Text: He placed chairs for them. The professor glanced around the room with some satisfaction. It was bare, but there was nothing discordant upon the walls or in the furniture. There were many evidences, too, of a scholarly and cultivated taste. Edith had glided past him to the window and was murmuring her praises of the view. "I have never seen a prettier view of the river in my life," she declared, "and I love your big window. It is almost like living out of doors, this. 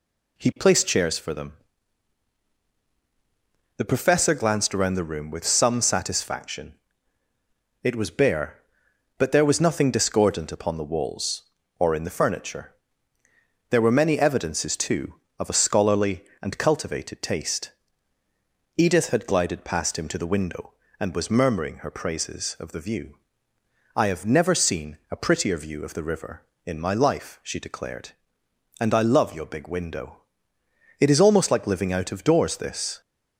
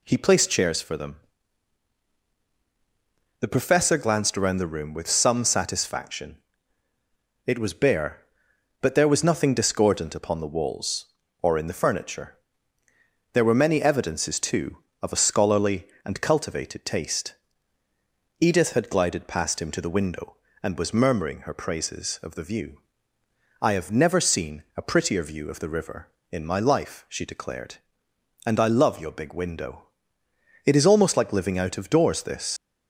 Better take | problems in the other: first | leaves "this" unfinished; at 32.5 s; 95 ms

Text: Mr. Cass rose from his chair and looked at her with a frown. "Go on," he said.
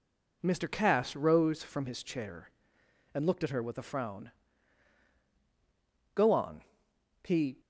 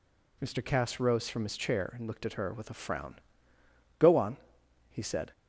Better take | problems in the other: second | stops before "said"; at 7.5 s

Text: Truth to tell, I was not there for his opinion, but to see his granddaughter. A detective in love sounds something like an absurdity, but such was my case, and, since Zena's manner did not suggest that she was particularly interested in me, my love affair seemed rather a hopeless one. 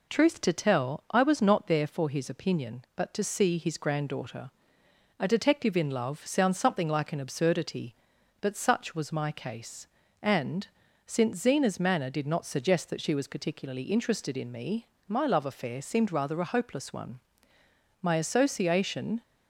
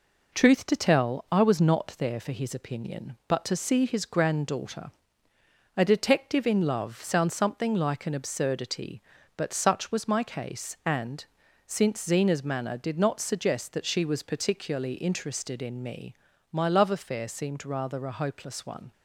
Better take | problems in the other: second | goes on to say "My association"; noticeable; from 18.0 s on; 1.2 s long

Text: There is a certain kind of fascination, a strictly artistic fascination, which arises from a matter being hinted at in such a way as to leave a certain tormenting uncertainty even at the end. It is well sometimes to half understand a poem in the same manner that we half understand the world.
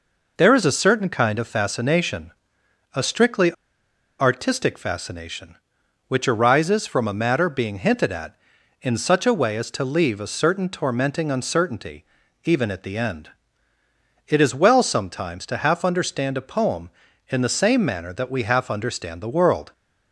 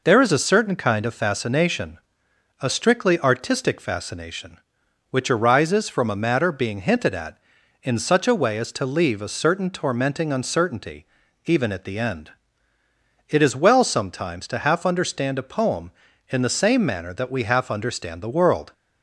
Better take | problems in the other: second | pauses between "strictly" and "artistic"; noticeable; at 3.5 s; 0.65 s long // pauses between "uncertainty" and "even"; at 12.0 s; 0.40 s long; also in the second

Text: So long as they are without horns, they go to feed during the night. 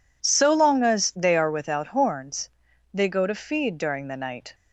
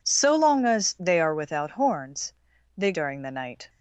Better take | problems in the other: first | skips "go to feed"; at 2.9 s

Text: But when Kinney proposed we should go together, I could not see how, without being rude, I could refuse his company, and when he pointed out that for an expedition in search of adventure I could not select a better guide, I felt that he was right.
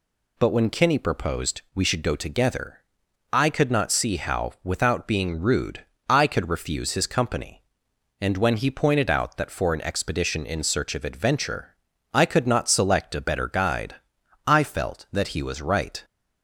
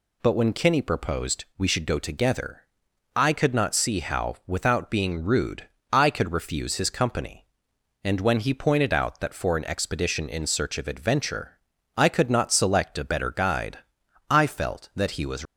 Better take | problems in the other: first | pauses between "adventure" and "I"; at 11.5 s; 0.38 s long; also in the first // stops before "right"; at 15.4 s

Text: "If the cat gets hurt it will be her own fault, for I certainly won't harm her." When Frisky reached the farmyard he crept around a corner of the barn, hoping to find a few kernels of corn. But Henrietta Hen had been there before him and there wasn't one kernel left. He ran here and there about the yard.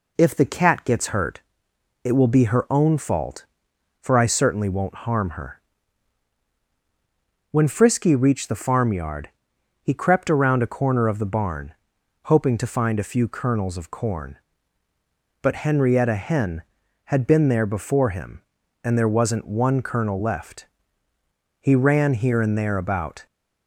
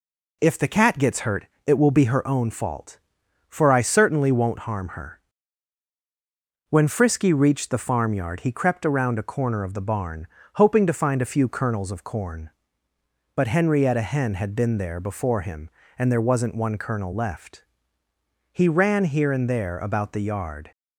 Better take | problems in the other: second | pauses between "hurt" and "it"; noticeable; at 1.4 s; 0.62 s long; slight in the second // pauses between "farmyard" and "he"; noticeable; at 9.2 s; 0.54 s long // stops before "the yard"; at 23.2 s

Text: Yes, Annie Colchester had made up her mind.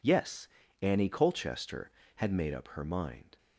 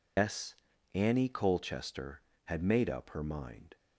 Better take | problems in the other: first | loses the start of "Yes"; at 0.1 s; 135 ms

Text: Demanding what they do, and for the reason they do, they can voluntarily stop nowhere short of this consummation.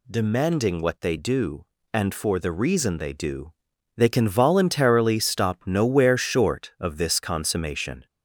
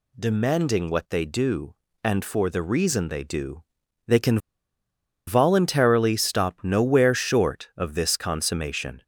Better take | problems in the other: first | pauses between "can" and "voluntarily"; noticeable; at 4.3 s; 0.88 s long

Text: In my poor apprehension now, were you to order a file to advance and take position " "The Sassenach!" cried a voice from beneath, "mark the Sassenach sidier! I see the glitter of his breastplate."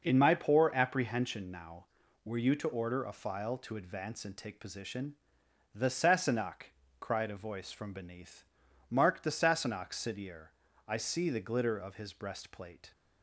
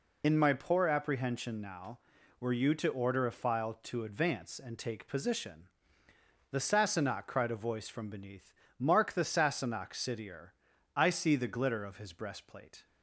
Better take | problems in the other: first | loses the start of "In"; at 0.2 s; 60 ms

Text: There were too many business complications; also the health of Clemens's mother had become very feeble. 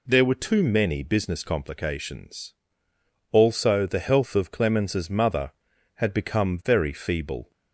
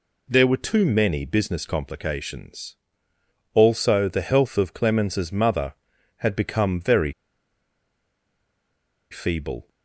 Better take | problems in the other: first | pauses between "very" and "feeble"; strong; at 7.1 s; 1.9 s long

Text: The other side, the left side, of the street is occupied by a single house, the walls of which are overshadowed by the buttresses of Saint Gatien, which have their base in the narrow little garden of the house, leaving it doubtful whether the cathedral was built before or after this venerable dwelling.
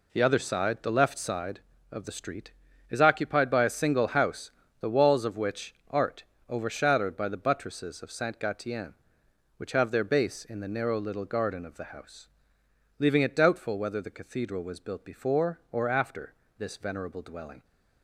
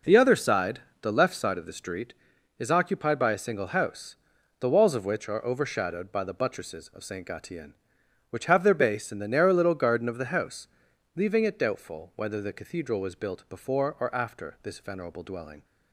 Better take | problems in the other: second | says "art" for "are"; at 5.8 s // pauses between "after" and "this"; slight; at 16.3 s; 0.24 s long

